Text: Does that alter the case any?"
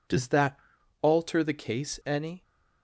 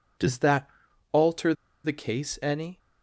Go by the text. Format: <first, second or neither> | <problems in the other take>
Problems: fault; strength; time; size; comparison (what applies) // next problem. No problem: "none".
first | pauses between "that" and "alter"; at 0.6 s; 0.42 s long; also in the first // pauses between "alter" and "the"; slight; at 1.5 s; 0.30 s long